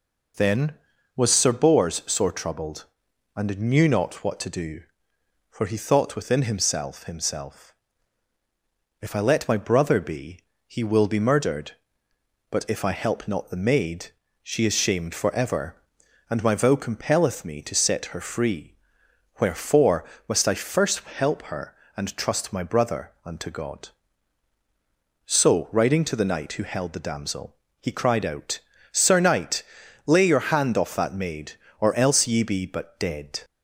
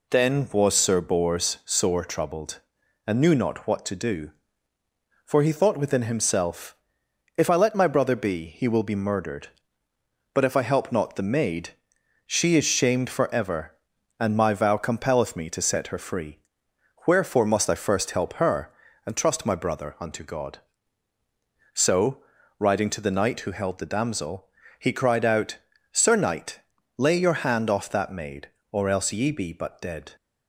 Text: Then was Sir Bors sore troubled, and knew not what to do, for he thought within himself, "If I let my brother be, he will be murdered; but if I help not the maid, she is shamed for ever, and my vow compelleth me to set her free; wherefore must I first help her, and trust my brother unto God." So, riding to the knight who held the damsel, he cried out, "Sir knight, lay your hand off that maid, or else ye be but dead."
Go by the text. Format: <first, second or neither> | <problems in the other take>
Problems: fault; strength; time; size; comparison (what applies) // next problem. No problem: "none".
second | says "himself" twice; at 7.0 s // pauses between "wherefore" and "must"; slight; at 20.0 s; 0.24 s long